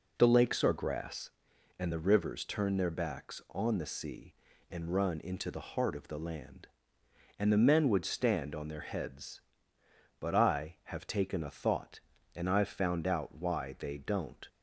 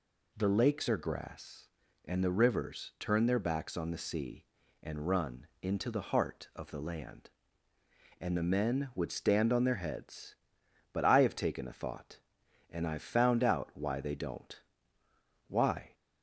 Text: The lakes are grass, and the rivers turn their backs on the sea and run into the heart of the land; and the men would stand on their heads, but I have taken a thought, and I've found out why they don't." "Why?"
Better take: second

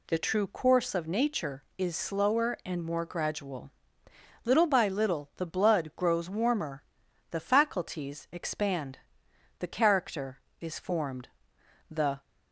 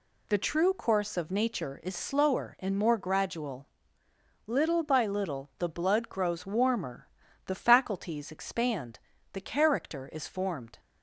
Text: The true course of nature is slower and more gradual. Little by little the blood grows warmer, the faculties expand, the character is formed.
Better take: second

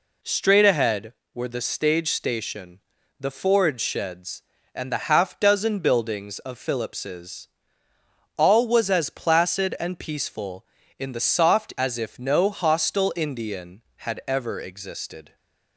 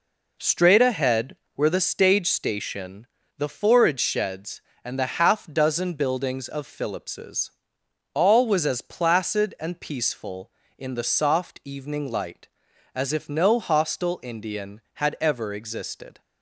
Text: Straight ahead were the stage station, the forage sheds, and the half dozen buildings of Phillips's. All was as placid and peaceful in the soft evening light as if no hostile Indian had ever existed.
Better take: second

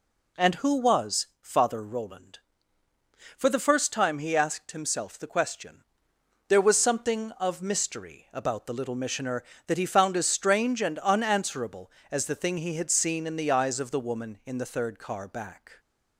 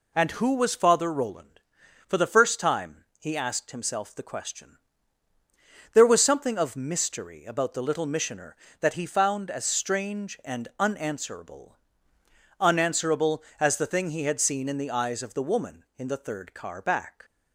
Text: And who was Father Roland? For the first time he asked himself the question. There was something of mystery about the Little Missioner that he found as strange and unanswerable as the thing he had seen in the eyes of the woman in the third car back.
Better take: first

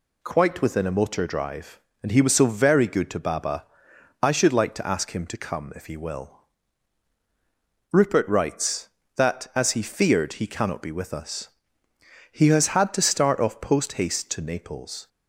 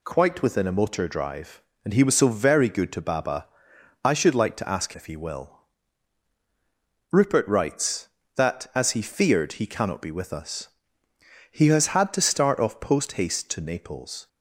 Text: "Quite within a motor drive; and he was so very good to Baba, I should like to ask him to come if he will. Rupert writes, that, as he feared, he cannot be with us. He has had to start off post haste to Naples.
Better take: first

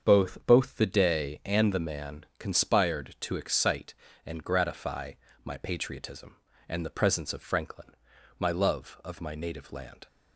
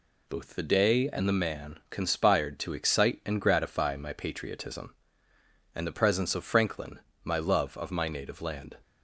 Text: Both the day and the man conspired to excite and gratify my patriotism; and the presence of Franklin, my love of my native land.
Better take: second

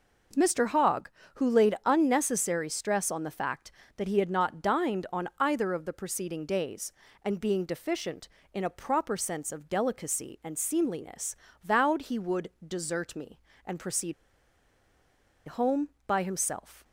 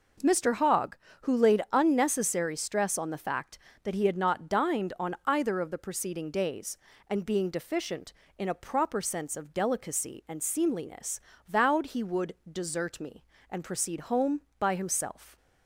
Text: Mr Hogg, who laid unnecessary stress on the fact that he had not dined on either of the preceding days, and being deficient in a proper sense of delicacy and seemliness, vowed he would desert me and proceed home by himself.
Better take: second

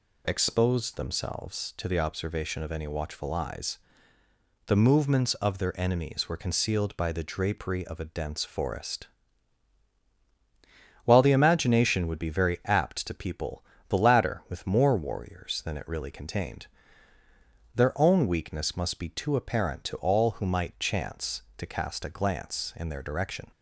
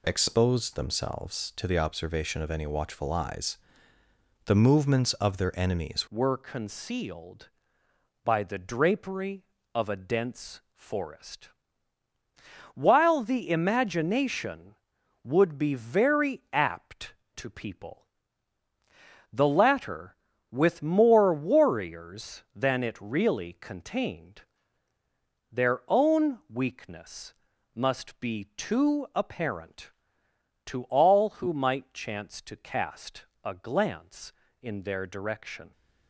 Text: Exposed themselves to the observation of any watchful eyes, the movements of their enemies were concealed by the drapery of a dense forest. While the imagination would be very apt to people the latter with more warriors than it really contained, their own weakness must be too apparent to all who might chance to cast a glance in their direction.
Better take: first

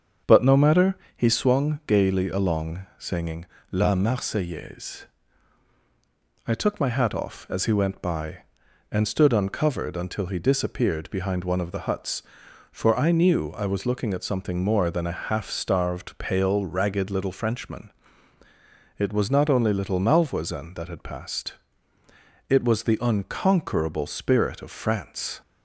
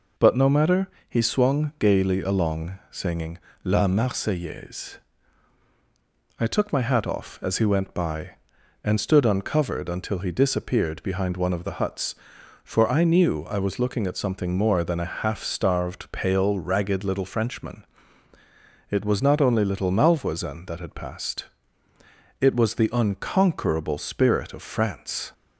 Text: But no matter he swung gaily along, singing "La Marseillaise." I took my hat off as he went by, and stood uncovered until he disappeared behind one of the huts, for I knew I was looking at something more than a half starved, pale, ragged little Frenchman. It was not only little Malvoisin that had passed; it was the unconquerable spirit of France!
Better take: second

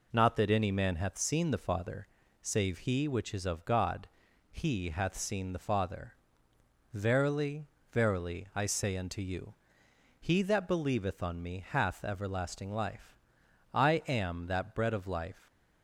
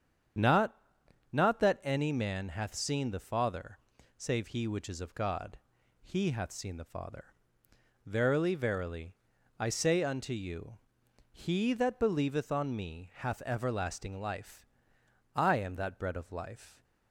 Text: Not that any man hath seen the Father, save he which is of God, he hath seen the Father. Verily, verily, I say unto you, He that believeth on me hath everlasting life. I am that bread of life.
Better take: first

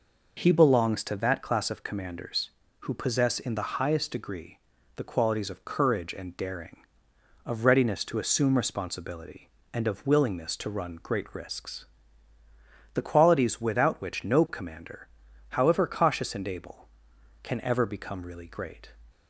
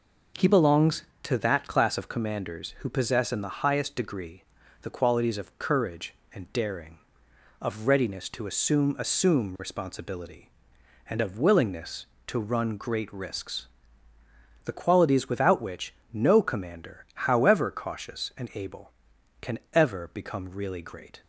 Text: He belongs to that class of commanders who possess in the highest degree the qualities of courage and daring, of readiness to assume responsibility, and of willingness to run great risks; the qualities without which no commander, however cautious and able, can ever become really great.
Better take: first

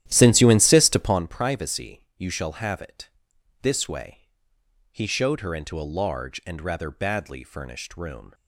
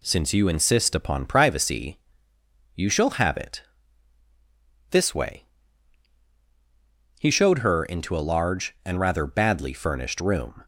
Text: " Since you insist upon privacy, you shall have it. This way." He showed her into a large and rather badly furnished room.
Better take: second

